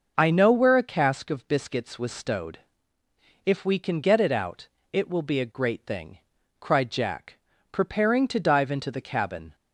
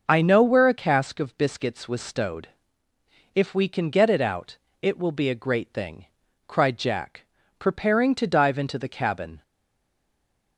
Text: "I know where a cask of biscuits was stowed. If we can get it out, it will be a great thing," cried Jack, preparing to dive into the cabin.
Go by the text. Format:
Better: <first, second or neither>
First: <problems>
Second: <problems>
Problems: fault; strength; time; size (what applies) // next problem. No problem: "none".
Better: first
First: none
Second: stays silent after the last word; noticeable; from 9.4 s on; 1.1 s long